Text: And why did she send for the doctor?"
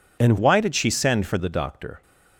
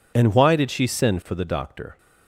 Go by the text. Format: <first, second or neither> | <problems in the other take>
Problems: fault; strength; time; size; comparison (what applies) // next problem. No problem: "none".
second | changes voice from "why" to "for"; from 0.3 to 1.3 s; 1.0 s long